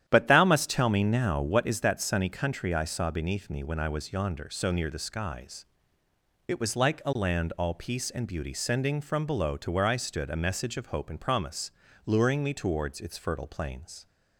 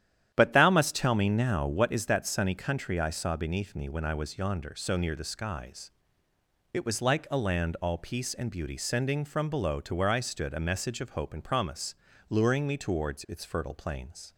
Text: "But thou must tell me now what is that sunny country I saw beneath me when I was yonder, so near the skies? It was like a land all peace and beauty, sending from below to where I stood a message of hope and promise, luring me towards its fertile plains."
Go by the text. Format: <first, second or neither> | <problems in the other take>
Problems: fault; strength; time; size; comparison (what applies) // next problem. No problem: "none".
neither | starts louder than the rest; strong; the same in both